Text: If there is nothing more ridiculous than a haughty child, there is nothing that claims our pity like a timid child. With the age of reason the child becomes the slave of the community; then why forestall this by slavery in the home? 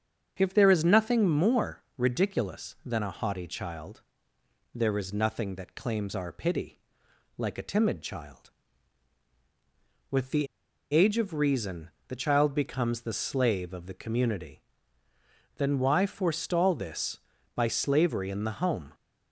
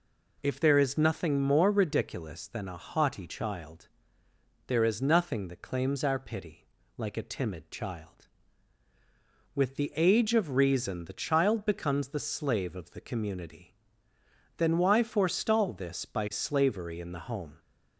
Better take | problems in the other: second | starts louder than the rest; strong; until 1.3 s; 7.5 dB // pauses between "more" and "ridiculous"; slight; at 1.8 s; 0.16 s long // pauses between "pity" and "like"; noticeable; at 6.7 s; 0.60 s long; slight in the second // pauses between "the" and "age"; at 10.4 s; 0.45 s long // pauses between "reason" and "the"; slight; at 11.8 s; 0.18 s long

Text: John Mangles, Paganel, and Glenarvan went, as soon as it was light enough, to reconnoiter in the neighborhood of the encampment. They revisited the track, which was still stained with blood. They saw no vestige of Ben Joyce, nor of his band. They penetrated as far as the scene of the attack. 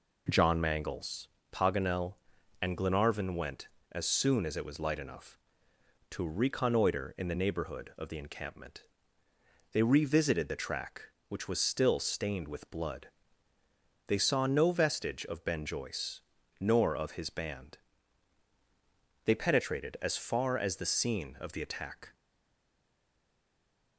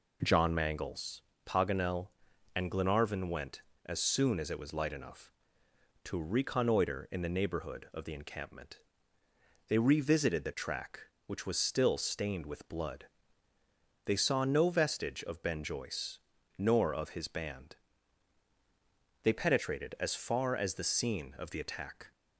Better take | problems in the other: second | stays silent after the last word; noticeable; from 22.1 s on; 1.8 s long

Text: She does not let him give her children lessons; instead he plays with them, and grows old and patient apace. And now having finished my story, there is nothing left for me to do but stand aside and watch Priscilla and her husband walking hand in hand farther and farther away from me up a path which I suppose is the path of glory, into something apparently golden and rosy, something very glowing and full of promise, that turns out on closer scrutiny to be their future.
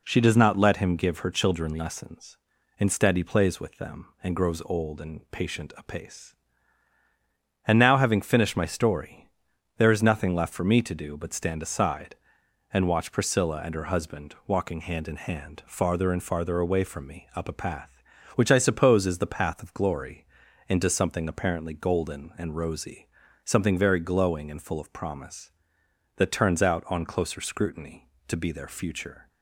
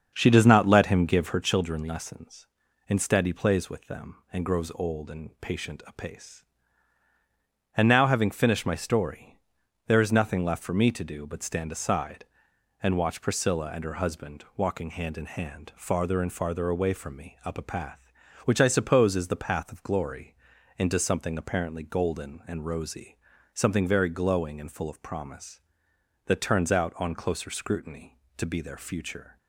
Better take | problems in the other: first | starts louder than the rest; until 1.6 s; 7 dB

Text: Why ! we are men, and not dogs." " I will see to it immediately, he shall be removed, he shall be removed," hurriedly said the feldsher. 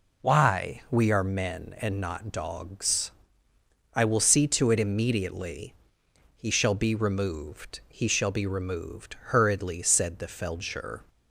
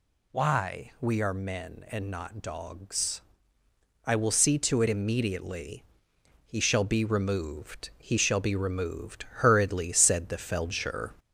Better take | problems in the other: first | gets louder; noticeable; throughout; 6 dB

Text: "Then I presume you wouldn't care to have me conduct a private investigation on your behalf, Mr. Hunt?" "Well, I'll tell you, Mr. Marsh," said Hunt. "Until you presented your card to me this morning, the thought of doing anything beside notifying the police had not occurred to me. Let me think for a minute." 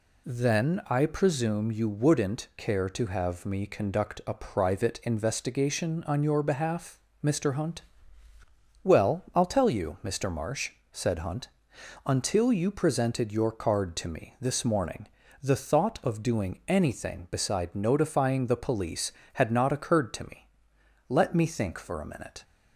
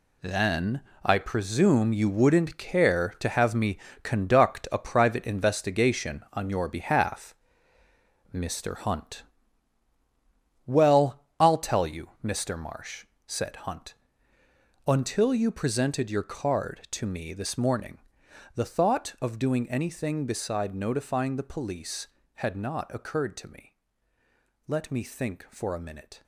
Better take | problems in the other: first | gets quieter; strong; throughout; 10 dB // pauses between "Then" and "I"; slight; at 0.8 s; 0.24 s long // pauses between "me" and "conduct"; slight; at 3.7 s; 0.26 s long

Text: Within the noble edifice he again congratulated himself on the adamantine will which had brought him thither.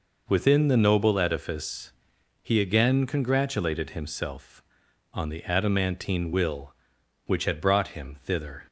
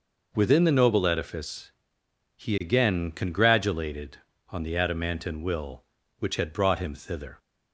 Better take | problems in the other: first | pauses between "edifice" and "he"; noticeable; at 1.7 s; 0.66 s long; noticeable in the first // skips "himself"; at 4.3 s

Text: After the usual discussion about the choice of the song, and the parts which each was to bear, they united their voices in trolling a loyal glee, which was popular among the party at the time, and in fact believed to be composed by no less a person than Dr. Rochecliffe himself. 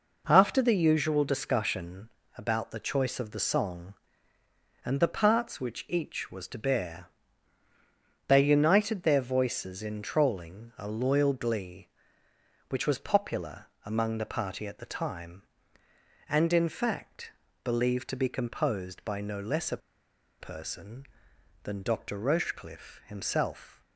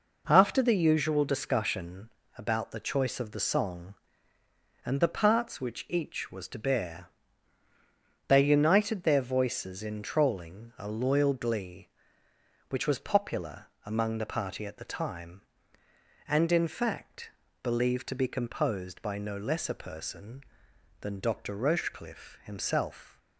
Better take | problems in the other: second | pauses between "discussion" and "about"; slight; at 2.0 s; 0.26 s long; slight in the second // pauses between "popular" and "among"; slight; at 13.6 s; 0.16 s long; slight in the second // pauses between "fact" and "believed"; slight; at 17.2 s; 0.34 s long; slight in the second // pauses between "a" and "person"; noticeable; at 19.7 s; 0.62 s long

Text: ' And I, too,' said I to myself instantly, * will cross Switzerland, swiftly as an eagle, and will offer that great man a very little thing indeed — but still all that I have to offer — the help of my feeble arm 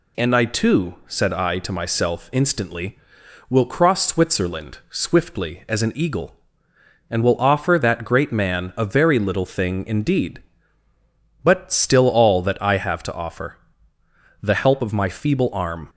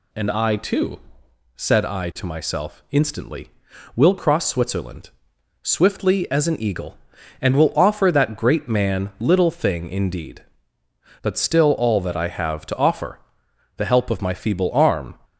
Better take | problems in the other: first | skips "a very"; at 9.1 s

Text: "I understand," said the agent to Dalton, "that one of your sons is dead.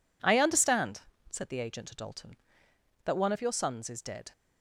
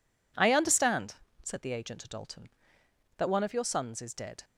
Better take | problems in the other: neither | none

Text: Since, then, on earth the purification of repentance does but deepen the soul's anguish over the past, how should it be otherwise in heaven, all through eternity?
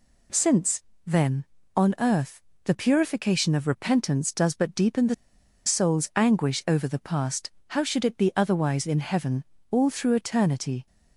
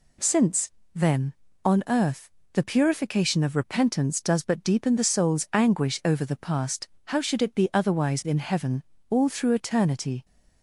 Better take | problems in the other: second | pauses between "earth" and "the"; slight; at 2.4 s; 0.22 s long; slight in the second // pauses between "the" and "soul's"; noticeable; at 5.1 s; 0.51 s long

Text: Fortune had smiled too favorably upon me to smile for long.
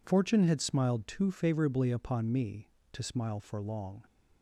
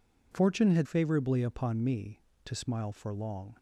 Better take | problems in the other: first | skips "smiled too"; at 0.8 s

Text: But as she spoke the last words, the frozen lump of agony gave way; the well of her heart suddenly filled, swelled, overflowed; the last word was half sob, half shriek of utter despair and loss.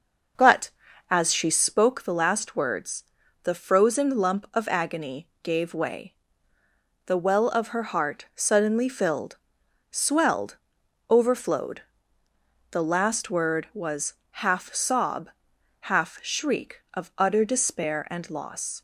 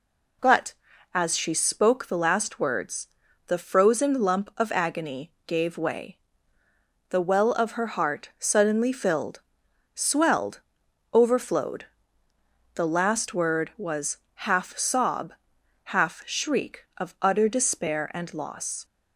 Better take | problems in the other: second | starts louder than the rest; noticeable; until 1.8 s; 5.5 dB // pauses between "agony" and "gave"; slight; at 5.2 s; 0.16 s long; slight in the second // pauses between "was" and "half"; slight; at 14.1 s; 0.16 s long; slight in the second

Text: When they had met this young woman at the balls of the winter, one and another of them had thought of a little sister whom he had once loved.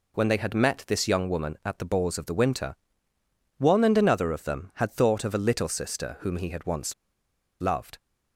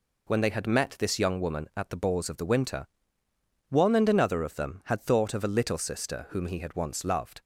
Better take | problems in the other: second | pauses between "once" and "loved"; noticeable; at 6.9 s; 0.67 s long

